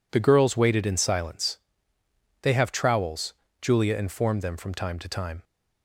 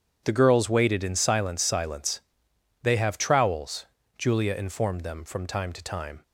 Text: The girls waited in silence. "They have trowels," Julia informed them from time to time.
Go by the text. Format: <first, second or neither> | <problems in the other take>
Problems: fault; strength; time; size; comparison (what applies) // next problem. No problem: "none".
first | starts louder than the rest; strong; until 1.2 s; 8.5 dB // says "silence" twice; at 1.6 s